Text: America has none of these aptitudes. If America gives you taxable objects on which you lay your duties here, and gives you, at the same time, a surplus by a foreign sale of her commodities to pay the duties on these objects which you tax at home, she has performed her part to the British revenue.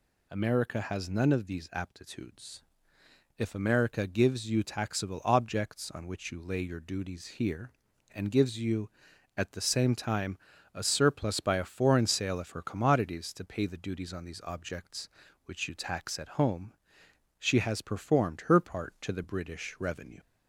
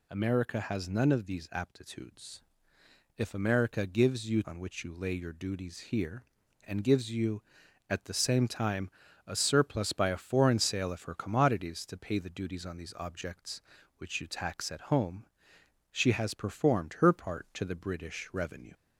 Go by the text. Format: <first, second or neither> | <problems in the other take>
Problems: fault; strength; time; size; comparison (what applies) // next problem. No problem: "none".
first | skips "taxable objects"; at 4.4 s